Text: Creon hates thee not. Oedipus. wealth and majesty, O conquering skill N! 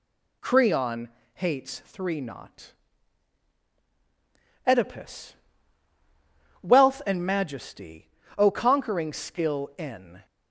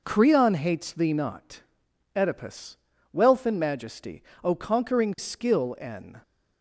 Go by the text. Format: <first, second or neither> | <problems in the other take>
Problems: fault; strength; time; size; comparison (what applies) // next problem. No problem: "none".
second | pauses between "Creon" and "hates"; slight; at 1.0 s; 0.26 s long // says "three" for "thee"; at 1.8 s